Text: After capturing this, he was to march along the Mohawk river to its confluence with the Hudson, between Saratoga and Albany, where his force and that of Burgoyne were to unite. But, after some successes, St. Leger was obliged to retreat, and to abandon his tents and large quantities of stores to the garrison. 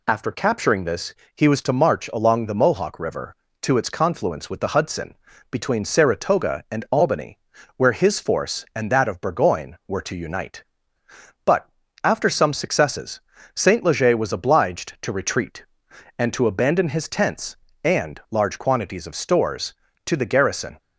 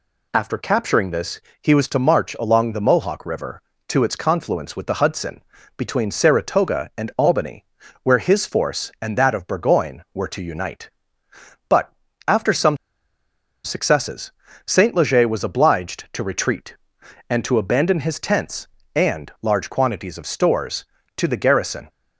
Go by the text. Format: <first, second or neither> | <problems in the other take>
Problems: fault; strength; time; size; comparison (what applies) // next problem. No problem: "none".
first | pauses between "some" and "successes"; noticeable; at 12.7 s; 0.87 s long